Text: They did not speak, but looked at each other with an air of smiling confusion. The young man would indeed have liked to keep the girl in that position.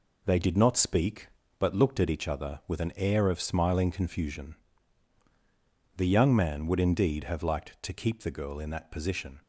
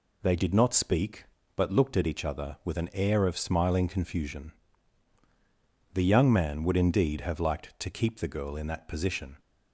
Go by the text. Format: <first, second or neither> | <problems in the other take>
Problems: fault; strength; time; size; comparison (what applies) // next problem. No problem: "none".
second | gets quieter; throughout; 7 dB